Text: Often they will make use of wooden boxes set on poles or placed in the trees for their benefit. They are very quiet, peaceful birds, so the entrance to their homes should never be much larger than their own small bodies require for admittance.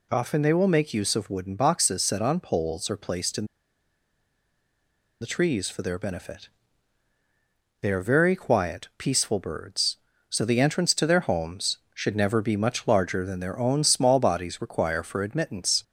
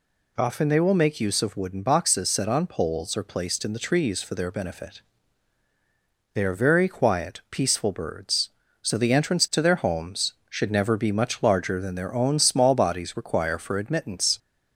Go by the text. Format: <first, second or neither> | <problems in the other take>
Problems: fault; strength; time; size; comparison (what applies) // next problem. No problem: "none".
second | pauses between "in" and "the"; strong; at 3.4 s; 1.7 s long